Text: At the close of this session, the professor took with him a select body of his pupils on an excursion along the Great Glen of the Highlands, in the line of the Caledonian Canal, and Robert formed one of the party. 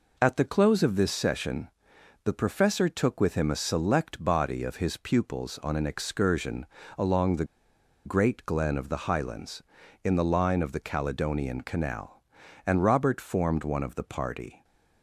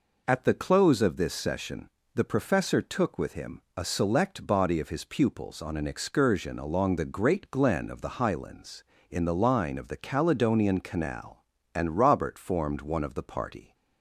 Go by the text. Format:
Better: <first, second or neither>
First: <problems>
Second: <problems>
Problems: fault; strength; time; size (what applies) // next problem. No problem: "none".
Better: second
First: pauses between "excursion" and "along"; slight; at 6.6 s; 0.32 s long // pauses between "the" and "Great"; noticeable; at 7.4 s; 0.60 s long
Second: none